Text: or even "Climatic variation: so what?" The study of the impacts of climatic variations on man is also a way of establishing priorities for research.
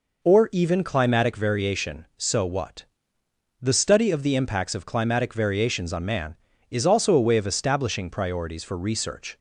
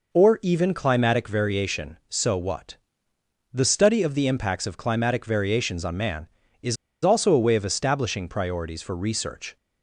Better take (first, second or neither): first